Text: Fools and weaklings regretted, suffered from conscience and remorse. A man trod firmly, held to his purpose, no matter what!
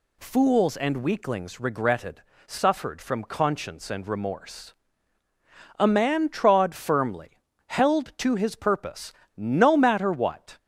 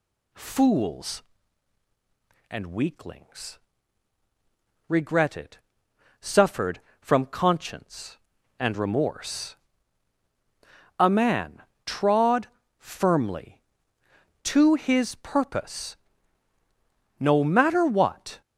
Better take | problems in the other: first | pauses between "weaklings" and "regretted"; strong; at 3.5 s; 1.3 s long // pauses between "man" and "trod"; slight; at 11.6 s; 0.22 s long // pauses between "trod" and "firmly"; slight; at 12.4 s; 0.30 s long // skips "held"; at 14.0 s

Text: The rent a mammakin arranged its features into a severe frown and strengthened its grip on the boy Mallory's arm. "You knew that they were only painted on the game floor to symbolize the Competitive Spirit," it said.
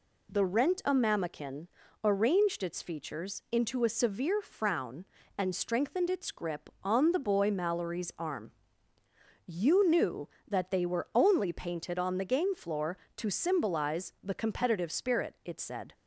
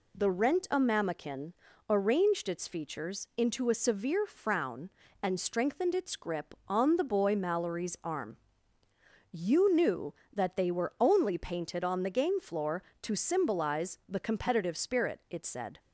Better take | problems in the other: neither | pauses between "mammakin" and "arranged"; the same in both

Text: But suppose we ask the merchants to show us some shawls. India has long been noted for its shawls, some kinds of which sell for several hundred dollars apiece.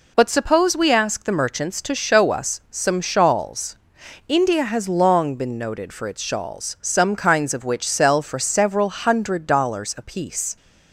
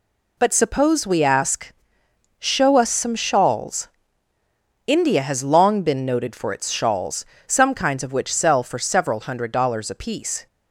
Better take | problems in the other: first | skips "the merchants to"; at 2.0 s

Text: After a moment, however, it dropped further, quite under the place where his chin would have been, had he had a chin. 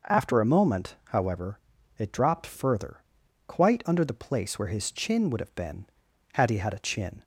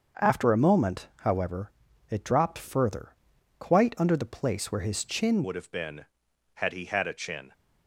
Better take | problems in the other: first | starts louder than the rest; until 1.2 s; 6.5 dB // changes voice at "would"; from 5.4 s on; 2.1 s long

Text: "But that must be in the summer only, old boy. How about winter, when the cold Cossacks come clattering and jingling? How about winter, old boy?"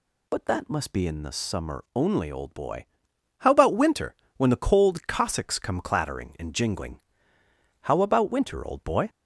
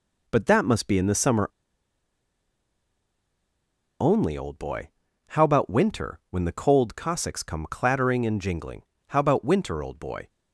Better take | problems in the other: first | pauses between "summer" and "only"; strong; at 1.4 s; 2.5 s long

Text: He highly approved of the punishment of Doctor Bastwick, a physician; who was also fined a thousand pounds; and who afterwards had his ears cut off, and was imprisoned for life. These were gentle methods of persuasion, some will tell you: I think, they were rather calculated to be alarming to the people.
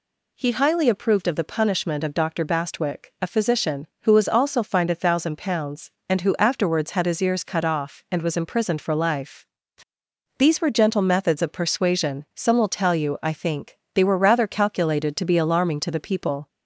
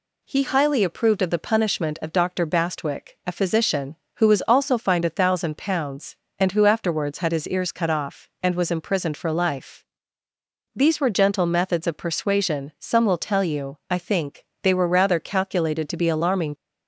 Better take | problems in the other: first | stops before "to the people"; at 16.5 s

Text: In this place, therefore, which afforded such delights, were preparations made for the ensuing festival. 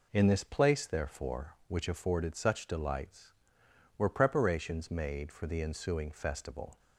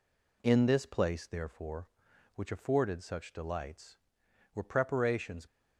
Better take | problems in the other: first | stops before "made for the ensuing festival"; at 5.4 s

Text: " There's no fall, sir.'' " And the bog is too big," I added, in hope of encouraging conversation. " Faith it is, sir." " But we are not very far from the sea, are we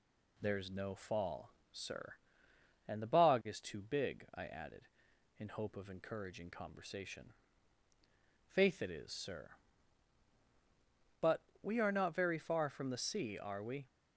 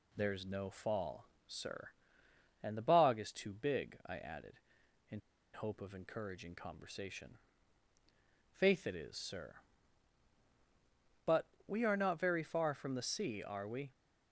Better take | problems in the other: first | pauses between "in" and "hope"; slight; at 5.2 s; 0.33 s long // pauses between "But" and "we"; slight; at 11.4 s; 0.20 s long; slight in the first

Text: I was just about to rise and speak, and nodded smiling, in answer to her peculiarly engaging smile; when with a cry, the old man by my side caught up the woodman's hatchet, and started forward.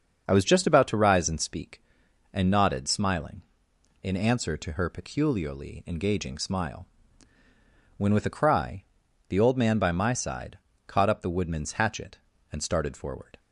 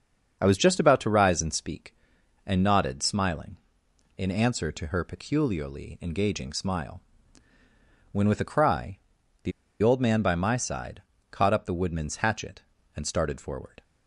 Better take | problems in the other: first | starts louder than the rest; until 1.4 s; 7 dB; also in the first // pauses between "the" and "old"; slight; at 9.5 s; 0.31 s long // pauses between "side" and "caught"; slight; at 11.0 s; 0.26 s long; slight in the first

